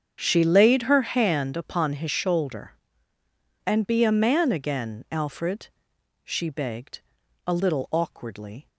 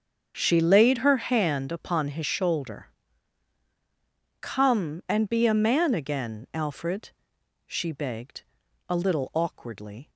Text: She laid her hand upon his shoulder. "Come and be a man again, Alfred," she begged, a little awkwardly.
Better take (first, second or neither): second